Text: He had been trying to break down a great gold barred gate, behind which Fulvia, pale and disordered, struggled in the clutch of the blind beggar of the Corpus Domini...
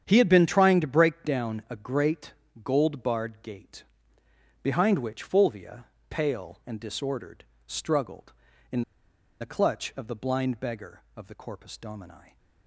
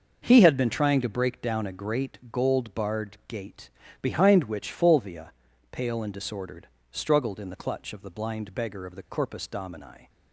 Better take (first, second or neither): second